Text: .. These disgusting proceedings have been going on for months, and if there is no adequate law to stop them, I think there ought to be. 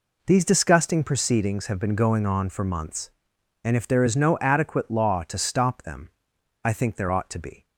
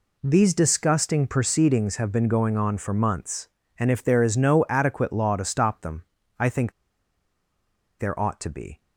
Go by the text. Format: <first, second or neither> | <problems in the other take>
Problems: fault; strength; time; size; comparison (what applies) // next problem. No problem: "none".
first | pauses between "think" and "there"; strong; at 6.7 s; 1.2 s long